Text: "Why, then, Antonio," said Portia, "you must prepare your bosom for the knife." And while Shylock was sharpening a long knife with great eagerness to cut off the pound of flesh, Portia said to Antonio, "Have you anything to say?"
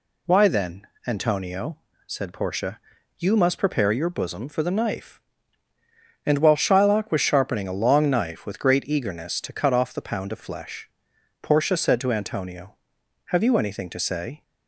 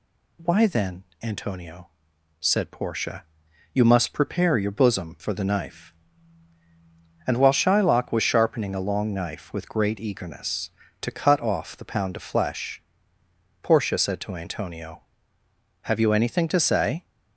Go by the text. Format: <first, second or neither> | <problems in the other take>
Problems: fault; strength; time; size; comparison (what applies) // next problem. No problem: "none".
neither | none